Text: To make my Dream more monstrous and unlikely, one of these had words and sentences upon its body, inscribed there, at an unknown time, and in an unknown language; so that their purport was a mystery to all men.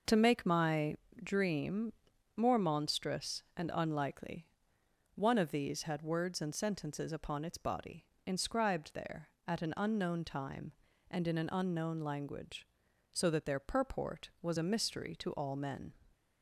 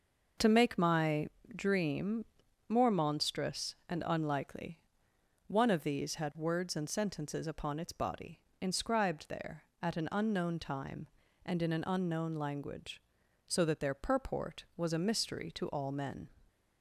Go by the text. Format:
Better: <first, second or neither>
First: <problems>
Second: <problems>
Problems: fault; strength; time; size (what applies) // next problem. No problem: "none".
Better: neither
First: pauses between "my" and "Dream"; slight; at 0.9 s; 0.28 s long // pauses between "Dream" and "more"; at 1.9 s; 0.42 s long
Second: pauses between "my" and "Dream"; slight; at 1.2 s; 0.28 s long // pauses between "Dream" and "more"; at 2.2 s; 0.42 s long